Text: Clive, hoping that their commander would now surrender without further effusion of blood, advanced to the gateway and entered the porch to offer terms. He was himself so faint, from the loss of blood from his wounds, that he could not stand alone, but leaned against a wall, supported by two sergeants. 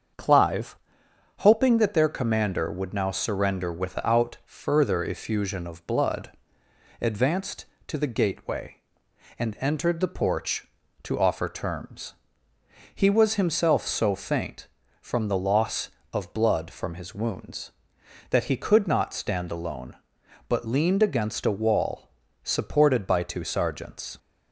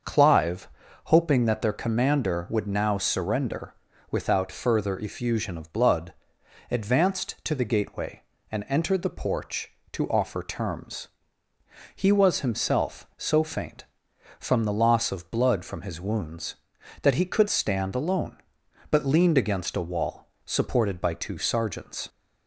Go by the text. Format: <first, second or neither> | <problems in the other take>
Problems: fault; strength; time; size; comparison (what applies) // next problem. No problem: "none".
first | starts louder than the rest; until 1.4 s; 6.5 dB; also in the first // pauses between "surrender" and "without"; slight; at 3.7 s; 0.36 s long // skips "not"; at 17.4 s